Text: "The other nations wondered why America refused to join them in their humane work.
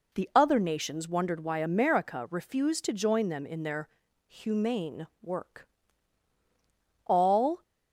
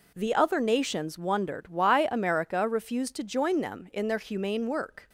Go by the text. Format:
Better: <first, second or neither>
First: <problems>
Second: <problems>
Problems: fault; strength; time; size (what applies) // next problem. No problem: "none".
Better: second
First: pauses between "their" and "humane"; at 3.8 s; 0.40 s long // pauses between "humane" and "work"; slight; at 5.0 s; 0.16 s long // goes on to say "All"; from 7.0 s on; 0.56 s long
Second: none